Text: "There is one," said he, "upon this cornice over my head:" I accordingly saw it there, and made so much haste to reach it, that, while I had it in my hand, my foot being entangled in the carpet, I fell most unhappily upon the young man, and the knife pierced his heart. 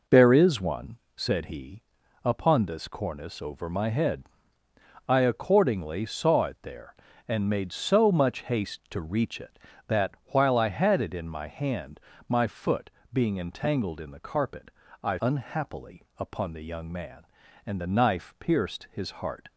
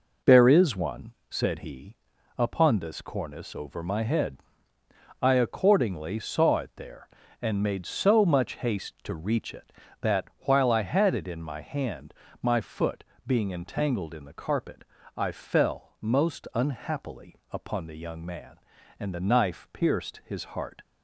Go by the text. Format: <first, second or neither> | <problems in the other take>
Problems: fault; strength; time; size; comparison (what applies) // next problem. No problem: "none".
second | pauses between "foot" and "being"; slight; at 12.8 s; 0.22 s long; slight in the second // skips "fell most"; at 15.1 s